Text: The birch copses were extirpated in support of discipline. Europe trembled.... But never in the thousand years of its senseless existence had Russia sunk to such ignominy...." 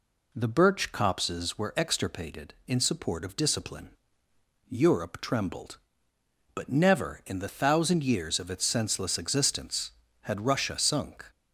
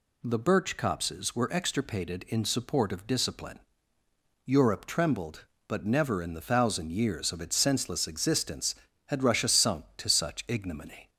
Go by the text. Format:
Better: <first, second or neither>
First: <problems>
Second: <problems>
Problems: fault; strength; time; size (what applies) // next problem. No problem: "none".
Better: second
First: stops before "to such ignominy"; at 11.3 s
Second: none